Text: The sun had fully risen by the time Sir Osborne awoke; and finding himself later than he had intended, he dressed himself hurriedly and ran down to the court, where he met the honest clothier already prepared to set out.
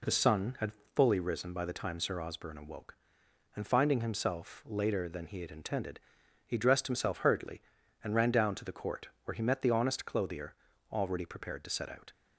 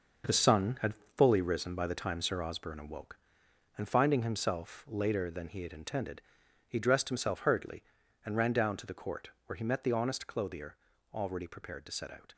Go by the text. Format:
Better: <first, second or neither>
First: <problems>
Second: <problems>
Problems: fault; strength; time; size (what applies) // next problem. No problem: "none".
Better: first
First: pauses between "had" and "fully"; slight; at 0.7 s; 0.22 s long // pauses between "clothier" and "already"; slight; at 10.5 s; 0.36 s long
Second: gets quieter; strong; throughout; 9 dB // pauses between "had" and "fully"; slight; at 0.9 s; 0.22 s long // pauses between "clothier" and "already"; slight; at 10.7 s; 0.36 s long